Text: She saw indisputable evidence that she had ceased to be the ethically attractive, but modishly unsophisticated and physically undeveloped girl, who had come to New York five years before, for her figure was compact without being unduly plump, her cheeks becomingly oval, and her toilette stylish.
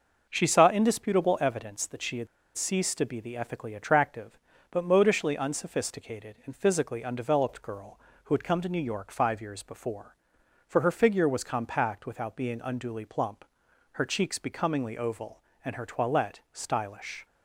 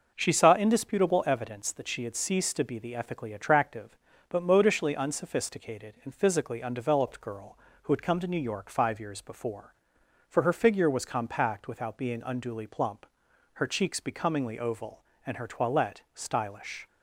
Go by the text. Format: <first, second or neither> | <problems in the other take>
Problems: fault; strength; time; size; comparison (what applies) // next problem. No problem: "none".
second | pauses between "had" and "ceased"; slight; at 2.2 s; 0.29 s long